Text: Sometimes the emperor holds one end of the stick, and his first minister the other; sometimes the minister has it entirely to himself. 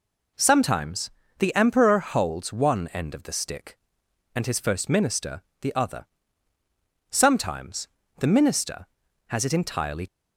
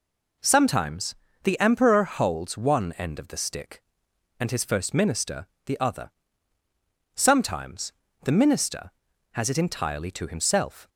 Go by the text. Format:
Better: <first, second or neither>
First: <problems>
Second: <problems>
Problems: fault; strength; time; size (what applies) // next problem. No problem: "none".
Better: second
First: pauses between "Sometimes" and "the"; slight; at 1.0 s; 0.30 s long // pauses between "minister" and "the"; slight; at 5.4 s; 0.18 s long // pauses between "sometimes" and "the"; slight; at 7.8 s; 0.32 s long // stops before "to himself"; at 10.0 s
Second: pauses between "Sometimes" and "the"; slight; at 1.1 s; 0.30 s long // pauses between "minister" and "the"; slight; at 5.4 s; 0.18 s long // pauses between "sometimes" and "the"; slight; at 7.9 s; 0.32 s long